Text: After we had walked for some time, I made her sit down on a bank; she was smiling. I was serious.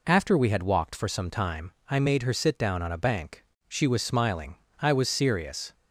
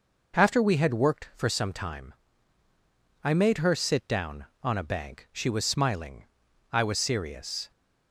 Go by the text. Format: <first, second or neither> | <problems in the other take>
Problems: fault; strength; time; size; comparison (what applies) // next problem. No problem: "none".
first | says "worked" for "walked"; at 0.9 s